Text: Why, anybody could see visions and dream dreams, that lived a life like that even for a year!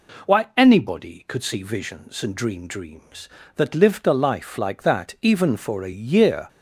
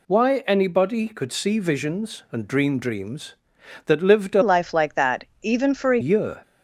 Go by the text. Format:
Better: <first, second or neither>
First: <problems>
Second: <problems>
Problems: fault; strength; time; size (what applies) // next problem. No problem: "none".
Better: first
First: none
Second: changes voice from "life" to "a"; from 4.4 to 6.0 s; 1.6 s long // pauses between "that" and "even"; slight; at 5.2 s; 0.18 s long